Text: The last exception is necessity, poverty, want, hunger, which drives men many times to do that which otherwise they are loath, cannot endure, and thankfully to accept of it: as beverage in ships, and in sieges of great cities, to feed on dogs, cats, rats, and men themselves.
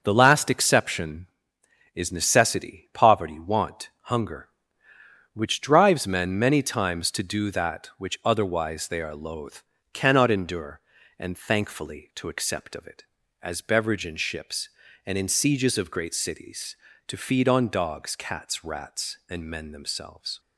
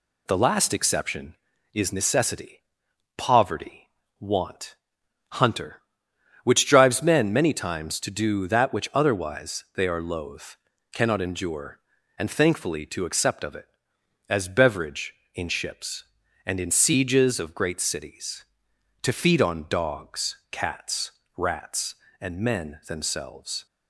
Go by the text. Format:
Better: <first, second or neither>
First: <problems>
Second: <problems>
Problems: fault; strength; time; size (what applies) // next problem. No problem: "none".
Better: first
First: none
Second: says "hunter" for "hunger"; at 5.2 s